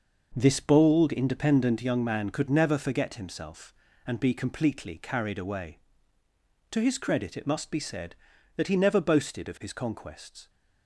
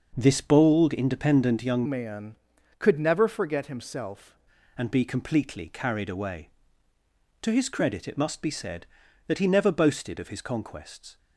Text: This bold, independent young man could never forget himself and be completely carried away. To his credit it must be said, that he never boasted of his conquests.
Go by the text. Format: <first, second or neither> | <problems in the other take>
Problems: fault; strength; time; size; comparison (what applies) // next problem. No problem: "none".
first | changes voice from "man" to "himself"; from 1.8 to 4.3 s; 2.5 s long